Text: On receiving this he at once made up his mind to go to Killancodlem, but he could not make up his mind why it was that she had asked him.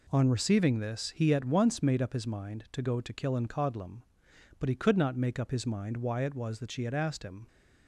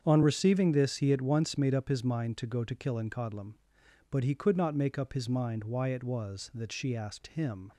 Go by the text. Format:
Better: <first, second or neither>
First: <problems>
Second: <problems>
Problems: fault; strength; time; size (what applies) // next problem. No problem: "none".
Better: first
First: none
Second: starts louder than the rest; strong; until 1.0 s; 7.5 dB // skips "had"; at 6.9 s